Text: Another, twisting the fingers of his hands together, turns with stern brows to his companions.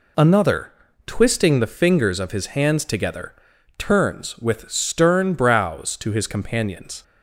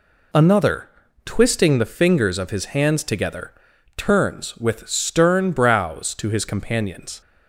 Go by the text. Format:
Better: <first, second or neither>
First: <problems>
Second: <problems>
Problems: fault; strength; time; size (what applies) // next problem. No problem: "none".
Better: neither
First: none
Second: none